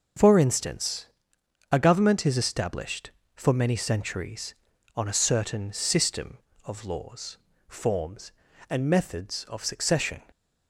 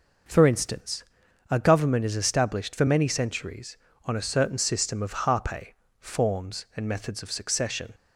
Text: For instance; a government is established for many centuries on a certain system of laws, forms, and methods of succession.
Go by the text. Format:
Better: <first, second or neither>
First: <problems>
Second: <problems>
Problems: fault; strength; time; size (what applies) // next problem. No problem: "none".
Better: first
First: none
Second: says "harpe" for "laws"; at 5.2 s